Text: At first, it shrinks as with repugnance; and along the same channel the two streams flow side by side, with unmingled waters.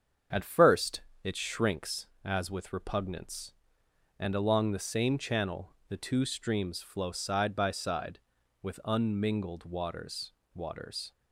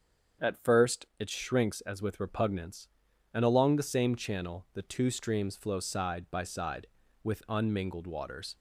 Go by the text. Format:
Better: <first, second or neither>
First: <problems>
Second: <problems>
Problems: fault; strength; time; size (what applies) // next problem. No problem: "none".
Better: second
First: starts louder than the rest; strong; until 1.5 s; 7 dB // pauses between "channel" and "the"; slight; at 5.7 s; 0.16 s long // says "waters" twice; at 10.5 s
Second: starts louder than the rest; strong; until 1.5 s; 7.5 dB